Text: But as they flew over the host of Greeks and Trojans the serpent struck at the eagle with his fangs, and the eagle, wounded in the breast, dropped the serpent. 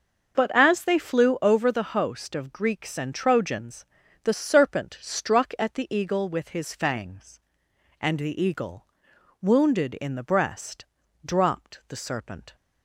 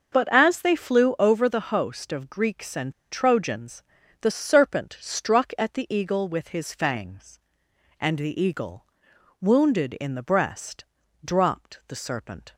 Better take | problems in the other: first | starts louder than the rest; until 1.1 s; 6.5 dB; also in the first // pauses between "and" and "Trojans"; slight; at 2.9 s; 0.19 s long // pauses between "Trojans" and "the"; at 3.8 s; 0.40 s long; also in the first

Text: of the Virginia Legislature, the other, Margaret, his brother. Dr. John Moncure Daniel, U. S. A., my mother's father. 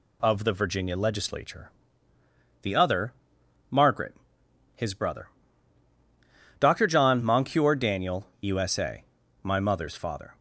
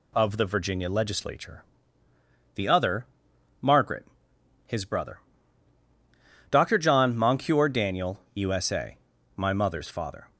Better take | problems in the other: neither | none

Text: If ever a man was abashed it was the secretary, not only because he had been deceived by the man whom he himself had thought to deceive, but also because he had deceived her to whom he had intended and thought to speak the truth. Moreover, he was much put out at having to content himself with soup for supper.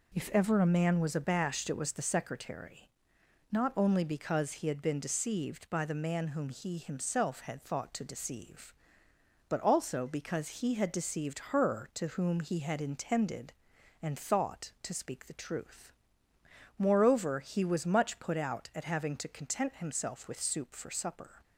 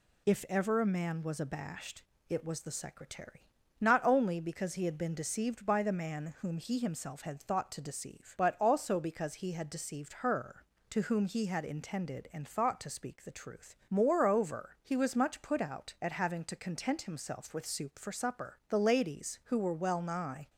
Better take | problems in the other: first | pauses between "abashed" and "it"; slight; at 2.0 s; 0.26 s long // goes on to say "The ladies who were well nigh"; strong; from 18.6 s on; 1.8 s long

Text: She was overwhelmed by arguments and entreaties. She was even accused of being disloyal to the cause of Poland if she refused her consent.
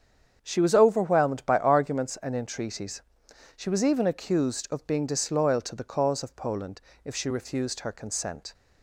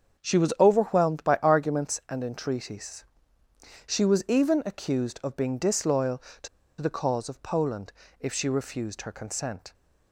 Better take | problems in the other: first | starts louder than the rest; strong; until 1.2 s; 7 dB; strong in the first // pauses between "to" and "the"; slight; at 6.4 s; 0.32 s long // pauses between "Poland" and "if"; slight; at 7.9 s; 0.30 s long; slight in the first

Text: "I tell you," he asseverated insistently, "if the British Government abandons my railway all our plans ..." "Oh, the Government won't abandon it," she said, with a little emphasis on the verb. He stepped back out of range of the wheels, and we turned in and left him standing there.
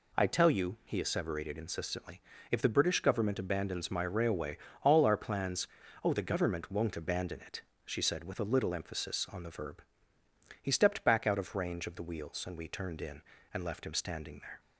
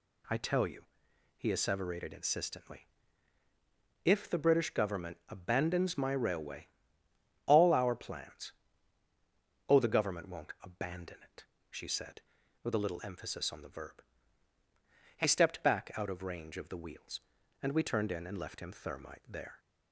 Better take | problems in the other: first | pauses between "railway" and "all"; noticeable; at 6.6 s; 0.78 s long; slight in the first // says "thermite" for "standing"; at 18.7 s

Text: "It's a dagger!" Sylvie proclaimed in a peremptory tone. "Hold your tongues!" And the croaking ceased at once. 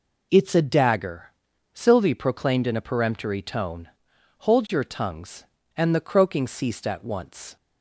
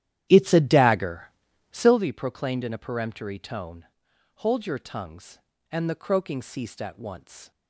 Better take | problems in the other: first | starts louder than the rest; strong; until 2.0 s; 11.5 dB

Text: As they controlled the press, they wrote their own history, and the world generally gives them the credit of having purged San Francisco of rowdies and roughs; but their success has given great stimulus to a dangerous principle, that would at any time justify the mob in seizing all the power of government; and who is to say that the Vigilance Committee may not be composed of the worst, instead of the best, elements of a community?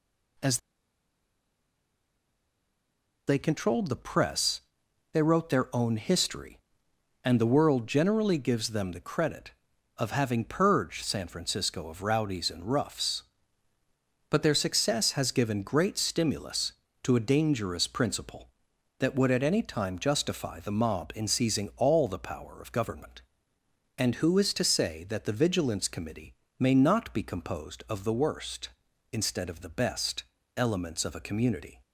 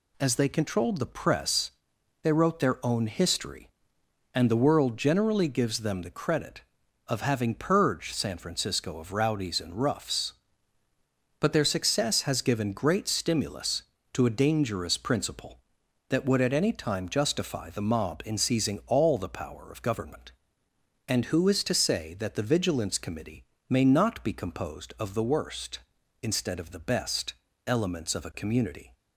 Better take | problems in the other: second | pauses between "As" and "they"; strong; at 0.5 s; 2.6 s long // pauses between "Committee" and "may"; slight; at 26.3 s; 0.24 s long; slight in the second

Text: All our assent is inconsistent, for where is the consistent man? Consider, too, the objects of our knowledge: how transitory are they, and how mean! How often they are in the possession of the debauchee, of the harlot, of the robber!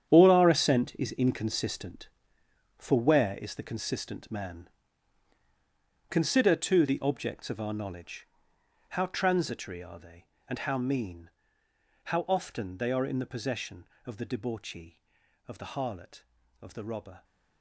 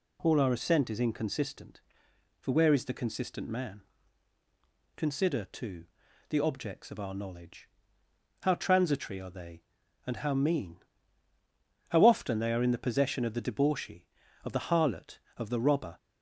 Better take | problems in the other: second | gets quieter; strong; throughout; 12.5 dB

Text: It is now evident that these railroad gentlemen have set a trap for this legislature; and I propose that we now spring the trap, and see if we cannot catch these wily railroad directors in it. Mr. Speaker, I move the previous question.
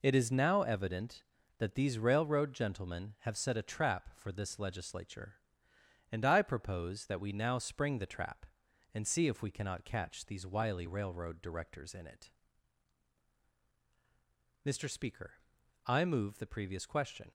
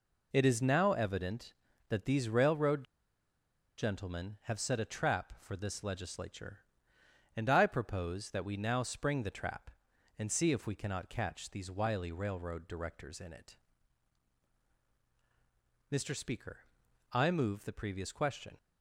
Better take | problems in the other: first | pauses between "railroad" and "gentlemen"; noticeable; at 2.8 s; 0.92 s long

